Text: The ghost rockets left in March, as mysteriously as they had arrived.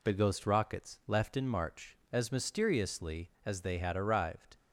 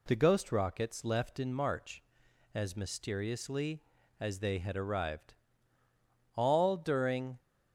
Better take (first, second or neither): first